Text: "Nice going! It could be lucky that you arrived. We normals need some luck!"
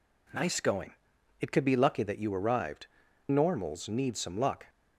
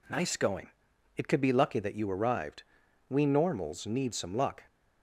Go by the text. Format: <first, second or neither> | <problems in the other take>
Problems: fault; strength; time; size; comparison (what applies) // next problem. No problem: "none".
second | skips "We"; at 3.0 s